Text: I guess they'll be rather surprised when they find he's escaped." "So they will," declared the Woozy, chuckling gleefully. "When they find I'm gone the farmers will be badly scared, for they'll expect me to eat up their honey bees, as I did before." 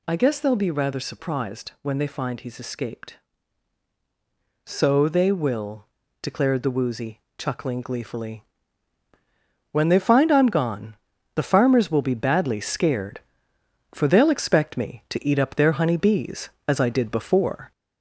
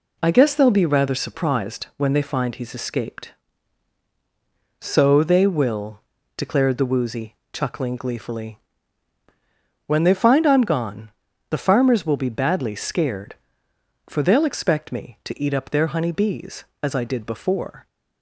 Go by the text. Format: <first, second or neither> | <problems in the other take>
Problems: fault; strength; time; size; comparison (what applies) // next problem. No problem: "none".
second | gets louder; slight; throughout; 3 dB // pauses between "gone" and "the"; at 10.9 s; 0.40 s long; also in the second